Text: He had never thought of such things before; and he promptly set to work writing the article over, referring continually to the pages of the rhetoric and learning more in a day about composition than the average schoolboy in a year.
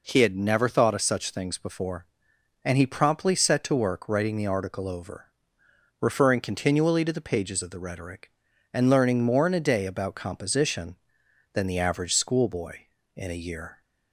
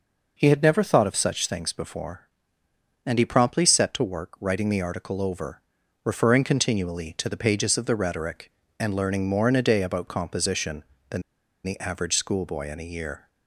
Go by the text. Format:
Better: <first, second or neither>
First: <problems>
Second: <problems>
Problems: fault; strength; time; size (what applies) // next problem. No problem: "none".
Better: first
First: none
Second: pauses between "than" and "the"; at 11.2 s; 0.43 s long